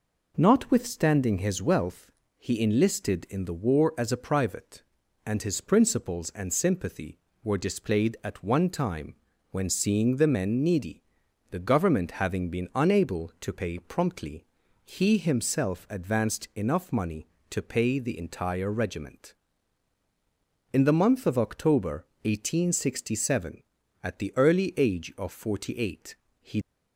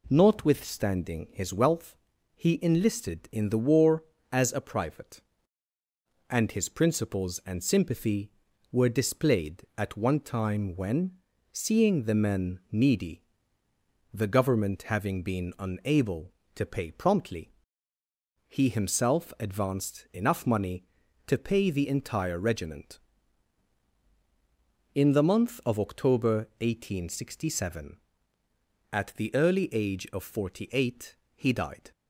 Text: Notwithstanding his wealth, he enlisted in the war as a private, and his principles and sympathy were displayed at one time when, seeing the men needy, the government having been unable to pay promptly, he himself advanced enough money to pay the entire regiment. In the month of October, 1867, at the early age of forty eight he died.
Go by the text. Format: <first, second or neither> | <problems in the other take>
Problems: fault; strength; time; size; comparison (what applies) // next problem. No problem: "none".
second | pauses between "time" and "when"; slight; at 9.1 s; 0.36 s long // pauses between "eight" and "he"; slight; at 26.1 s; 0.26 s long; slight in the second // stops before "died"; at 26.6 s